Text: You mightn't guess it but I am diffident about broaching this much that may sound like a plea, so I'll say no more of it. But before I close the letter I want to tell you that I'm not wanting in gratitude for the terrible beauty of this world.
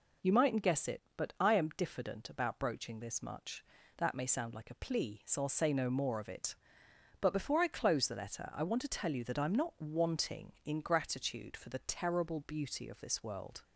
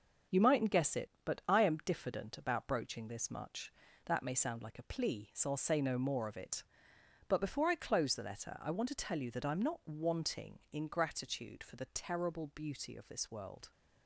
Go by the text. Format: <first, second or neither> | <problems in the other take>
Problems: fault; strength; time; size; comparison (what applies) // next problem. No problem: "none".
first | gets quieter; throughout; 6.5 dB